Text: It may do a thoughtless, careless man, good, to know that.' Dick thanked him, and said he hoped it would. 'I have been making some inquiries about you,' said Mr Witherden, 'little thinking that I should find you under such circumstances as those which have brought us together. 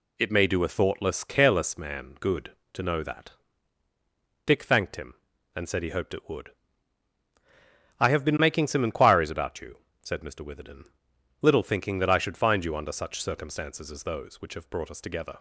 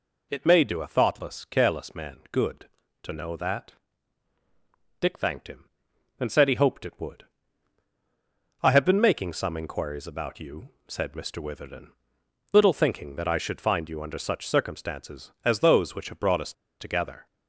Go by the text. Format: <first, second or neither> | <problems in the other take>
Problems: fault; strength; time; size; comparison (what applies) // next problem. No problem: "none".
first | pauses between "us" and "together"; slight; at 16.5 s; 0.27 s long